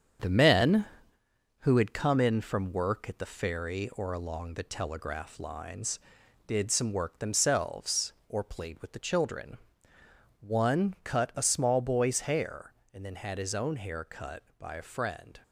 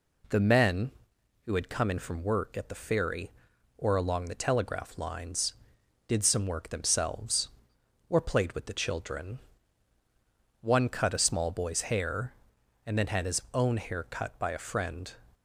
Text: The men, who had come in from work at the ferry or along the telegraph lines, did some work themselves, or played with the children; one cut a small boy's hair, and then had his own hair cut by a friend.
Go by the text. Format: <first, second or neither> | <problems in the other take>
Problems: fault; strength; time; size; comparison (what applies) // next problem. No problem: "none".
second | gets quieter; noticeable; throughout; 5.5 dB